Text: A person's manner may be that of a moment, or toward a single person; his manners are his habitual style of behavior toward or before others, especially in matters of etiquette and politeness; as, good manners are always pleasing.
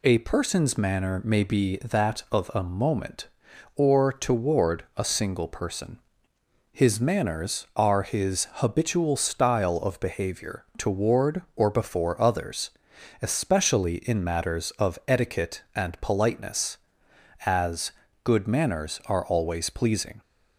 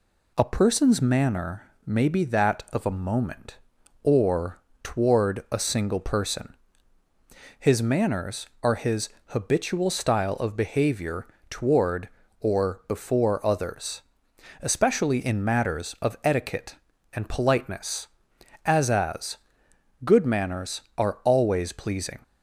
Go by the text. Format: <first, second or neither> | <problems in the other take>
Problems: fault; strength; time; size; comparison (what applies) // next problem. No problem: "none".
first | pauses between "manner" and "may"; slight; at 1.6 s; 0.16 s long // pauses between "or" and "toward"; slight; at 4.5 s; 0.22 s long // pauses between "his" and "habitual"; slight; at 9.0 s; 0.16 s long // pauses between "behavior" and "toward"; slight; at 11.2 s; 0.24 s long // says "as" twice; at 18.8 s